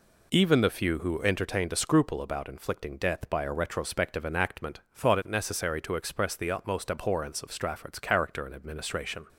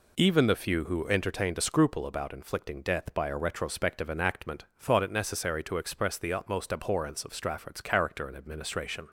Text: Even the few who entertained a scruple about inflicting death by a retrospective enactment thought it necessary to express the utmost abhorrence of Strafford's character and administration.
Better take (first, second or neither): neither